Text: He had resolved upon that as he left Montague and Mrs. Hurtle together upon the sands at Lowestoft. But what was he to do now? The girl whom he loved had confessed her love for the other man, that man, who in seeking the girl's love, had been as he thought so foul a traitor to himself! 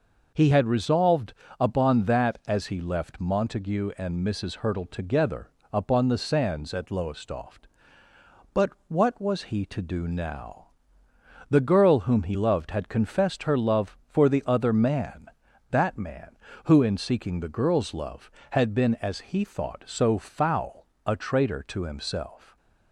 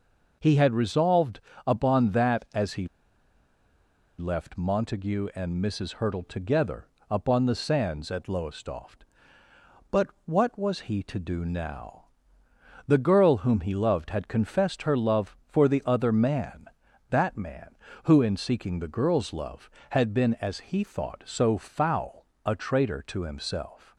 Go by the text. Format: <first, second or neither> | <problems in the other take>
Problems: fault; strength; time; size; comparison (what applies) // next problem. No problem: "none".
first | pauses between "resolved" and "upon"; slight; at 1.4 s; 0.26 s long; slight in the first // pauses between "he" and "left"; strong; at 2.8 s; 1.3 s long // pauses between "together" and "upon"; slight; at 6.8 s; 0.22 s long; slight in the first // pauses between "But" and "what"; slight; at 10.0 s; 0.18 s long; slight in the first // pauses between "foul" and "a"; slight; at 22.2 s; 0.20 s long; slight in the first